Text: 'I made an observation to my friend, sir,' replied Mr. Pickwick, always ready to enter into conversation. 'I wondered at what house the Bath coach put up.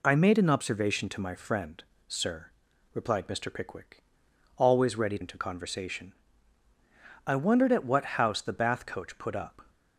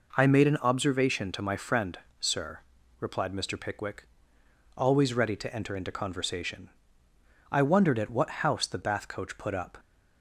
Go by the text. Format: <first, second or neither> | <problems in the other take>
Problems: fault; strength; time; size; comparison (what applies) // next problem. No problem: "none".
second | skips "to enter"; at 5.1 s